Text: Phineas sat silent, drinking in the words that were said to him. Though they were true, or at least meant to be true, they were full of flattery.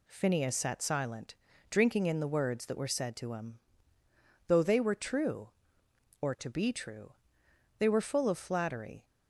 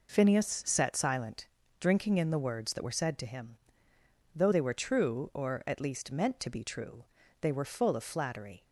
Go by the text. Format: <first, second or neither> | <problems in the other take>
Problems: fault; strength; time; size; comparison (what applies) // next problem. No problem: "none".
second | skips "at least meant"; at 6.3 s